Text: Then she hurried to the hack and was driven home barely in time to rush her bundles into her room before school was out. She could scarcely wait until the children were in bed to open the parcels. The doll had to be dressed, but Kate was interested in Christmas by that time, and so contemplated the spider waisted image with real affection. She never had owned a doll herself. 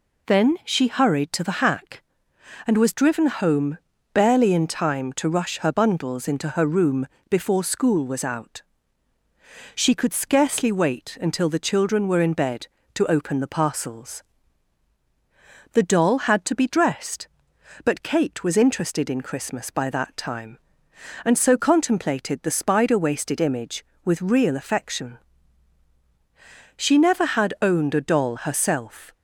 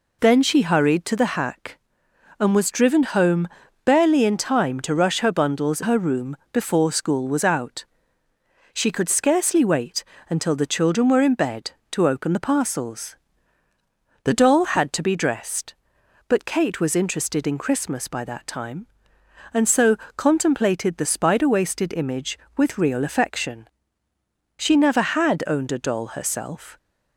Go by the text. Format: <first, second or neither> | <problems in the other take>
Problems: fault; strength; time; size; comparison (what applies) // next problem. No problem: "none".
first | pauses between "home" and "barely"; slight; at 3.4 s; 0.36 s long; slight in the first // skips "into"; at 5.8 s // pauses between "room" and "before"; slight; at 6.3 s; 0.16 s long; slight in the first // pauses between "wait" and "until"; slight; at 10.0 s; 0.26 s long // pauses between "so" and "contemplated"; slight; at 19.9 s; 0.18 s long